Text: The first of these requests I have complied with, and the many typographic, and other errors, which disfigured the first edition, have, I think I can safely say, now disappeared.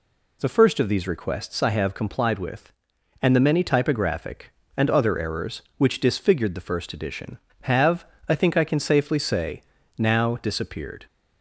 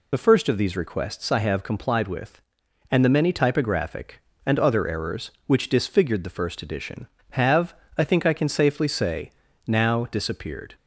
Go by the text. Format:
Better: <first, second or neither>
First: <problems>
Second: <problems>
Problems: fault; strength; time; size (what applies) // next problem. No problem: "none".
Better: first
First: none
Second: loses the start of "The"; at 0.1 s; 40 ms